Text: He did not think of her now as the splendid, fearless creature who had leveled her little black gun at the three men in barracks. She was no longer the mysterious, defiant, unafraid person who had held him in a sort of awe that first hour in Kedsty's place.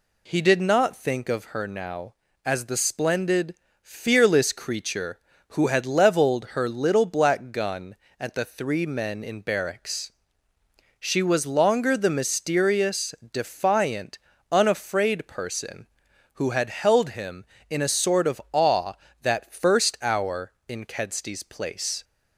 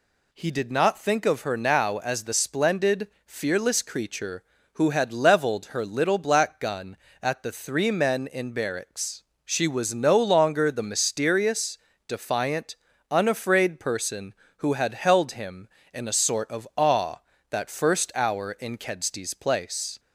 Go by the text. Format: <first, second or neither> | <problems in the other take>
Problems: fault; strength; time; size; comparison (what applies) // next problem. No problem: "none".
second | skips "no"; at 11.4 s